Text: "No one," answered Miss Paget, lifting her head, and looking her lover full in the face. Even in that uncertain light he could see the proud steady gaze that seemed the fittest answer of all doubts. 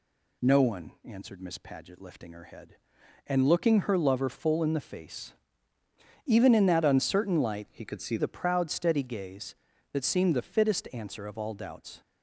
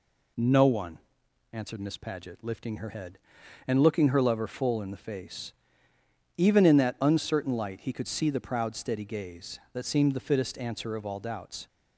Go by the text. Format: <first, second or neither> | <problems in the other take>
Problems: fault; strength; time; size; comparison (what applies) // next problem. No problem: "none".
second | changes voice from "he" to "see"; from 7.7 to 8.1 s; 0.4 s long